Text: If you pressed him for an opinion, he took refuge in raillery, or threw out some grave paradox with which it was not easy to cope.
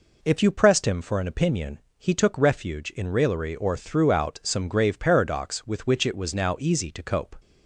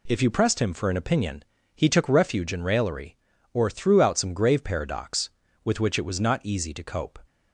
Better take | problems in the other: second | says "now" for "not"; at 6.3 s

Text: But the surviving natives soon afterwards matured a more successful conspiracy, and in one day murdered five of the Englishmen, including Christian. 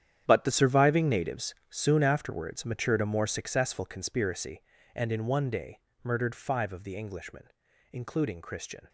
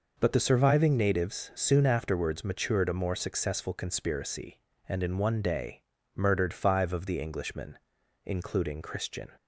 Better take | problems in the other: second | gets quieter; strong; throughout; 13.5 dB // pauses between "natives" and "soon"; slight; at 1.5 s; 0.16 s long // pauses between "day" and "murdered"; slight; at 5.7 s; 0.24 s long; slight in the second

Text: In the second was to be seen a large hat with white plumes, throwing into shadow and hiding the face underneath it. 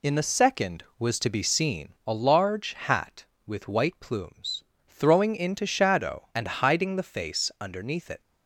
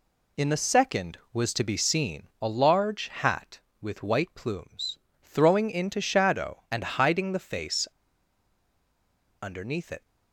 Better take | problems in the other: first | pauses between "face" and "underneath"; strong; at 7.8 s; 1.5 s long

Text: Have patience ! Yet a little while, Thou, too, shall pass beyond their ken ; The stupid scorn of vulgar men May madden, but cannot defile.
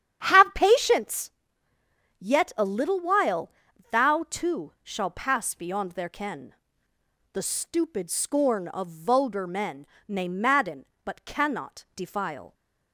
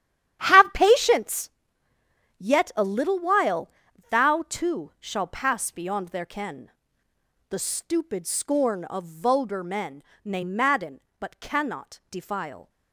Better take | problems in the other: first | gets quieter; strong; throughout; 14 dB // starts louder than the rest; strong; until 1.4 s; 11 dB; strong in the first // pauses between "men" and "May"; slight; at 10.0 s; 0.22 s long; slight in the first

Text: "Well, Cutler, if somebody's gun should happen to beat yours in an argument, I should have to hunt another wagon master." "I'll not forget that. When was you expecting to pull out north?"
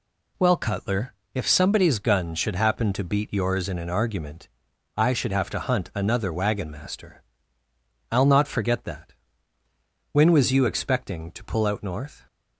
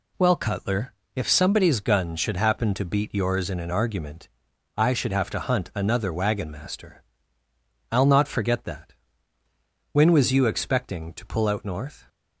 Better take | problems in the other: neither | none

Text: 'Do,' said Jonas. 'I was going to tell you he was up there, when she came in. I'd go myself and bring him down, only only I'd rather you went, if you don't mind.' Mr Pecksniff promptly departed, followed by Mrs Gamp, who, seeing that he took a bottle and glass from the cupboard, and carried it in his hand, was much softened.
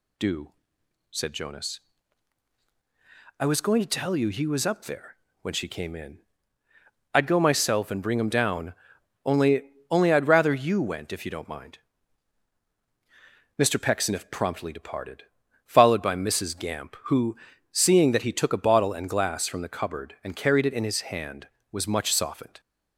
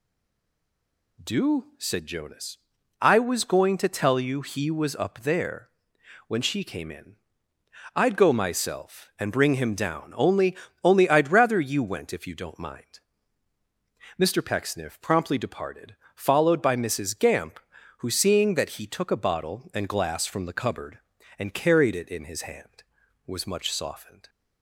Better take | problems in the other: first | stays silent before the first word; noticeable; until 1.1 s; 1.1 s long // pauses between "only" and "only"; slight; at 10.5 s; 0.26 s long; slight in the first

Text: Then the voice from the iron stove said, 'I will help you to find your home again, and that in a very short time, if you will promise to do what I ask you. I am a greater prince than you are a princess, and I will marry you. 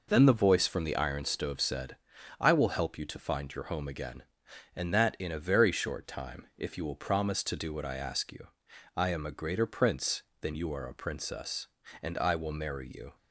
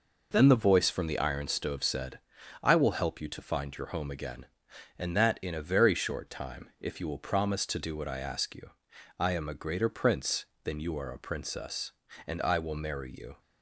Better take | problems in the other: neither | none

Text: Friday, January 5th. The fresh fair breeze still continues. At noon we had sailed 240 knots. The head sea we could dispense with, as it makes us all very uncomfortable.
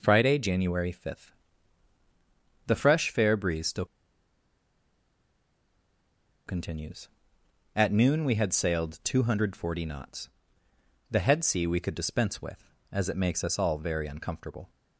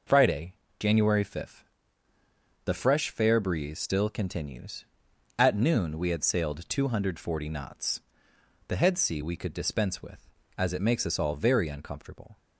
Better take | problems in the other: second | pauses between "still" and "continues"; strong; at 3.8 s; 2.6 s long

